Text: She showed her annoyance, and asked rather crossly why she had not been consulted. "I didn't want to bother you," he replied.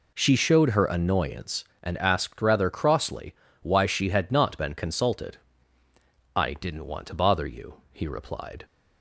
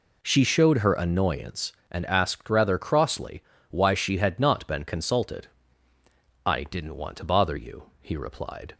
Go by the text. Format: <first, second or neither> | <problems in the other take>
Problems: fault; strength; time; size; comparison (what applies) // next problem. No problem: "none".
neither | pauses between "crossly" and "why"; slight; the same in both